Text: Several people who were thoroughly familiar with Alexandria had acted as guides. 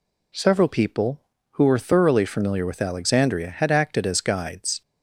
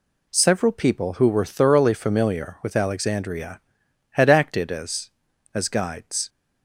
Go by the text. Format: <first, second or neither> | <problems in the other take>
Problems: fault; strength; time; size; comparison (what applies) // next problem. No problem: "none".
first | says "as" twice; at 5.5 s